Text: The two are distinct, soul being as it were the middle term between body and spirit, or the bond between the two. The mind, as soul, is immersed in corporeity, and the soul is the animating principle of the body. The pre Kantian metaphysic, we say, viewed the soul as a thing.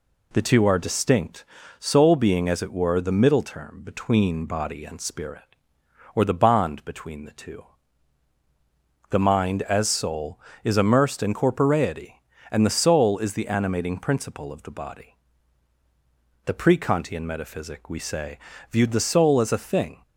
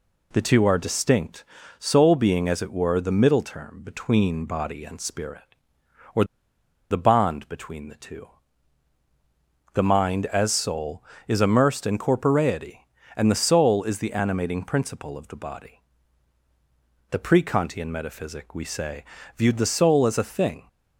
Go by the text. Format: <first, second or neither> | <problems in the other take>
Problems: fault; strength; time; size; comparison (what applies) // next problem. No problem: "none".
first | pauses between "or" and "the"; noticeable; at 6.2 s; 0.67 s long